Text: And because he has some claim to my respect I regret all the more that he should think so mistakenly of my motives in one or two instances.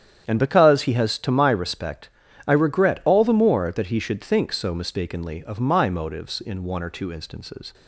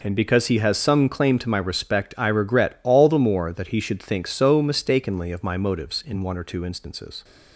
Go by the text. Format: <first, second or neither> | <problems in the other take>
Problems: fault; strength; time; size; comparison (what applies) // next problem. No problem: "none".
second | starts louder than the rest; strong; until 1.3 s; 9 dB // skips "some claim"; at 1.1 s // pauses between "respect" and "I"; at 2.0 s; 0.38 s long